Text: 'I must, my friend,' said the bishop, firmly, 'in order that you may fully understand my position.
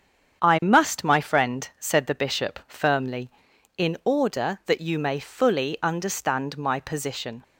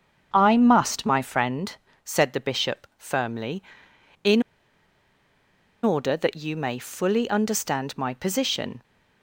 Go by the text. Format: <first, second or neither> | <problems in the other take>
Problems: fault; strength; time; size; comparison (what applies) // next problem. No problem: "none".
first | starts louder than the rest; strong; until 1.3 s; 7.5 dB; strong in the first // pauses between "in" and "order"; strong; at 4.4 s; 1.4 s long